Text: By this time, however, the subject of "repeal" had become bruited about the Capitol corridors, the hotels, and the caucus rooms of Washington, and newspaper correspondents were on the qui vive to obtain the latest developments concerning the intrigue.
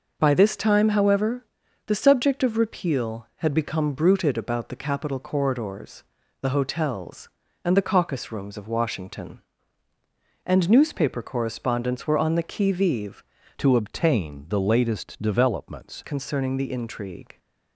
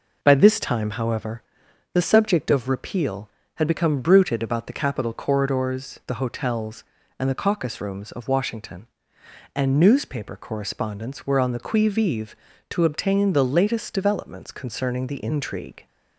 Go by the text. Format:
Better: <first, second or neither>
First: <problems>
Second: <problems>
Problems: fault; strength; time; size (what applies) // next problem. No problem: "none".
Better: second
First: changes voice from "to" to "developments"; from 13.5 to 16.0 s; 2.5 s long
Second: none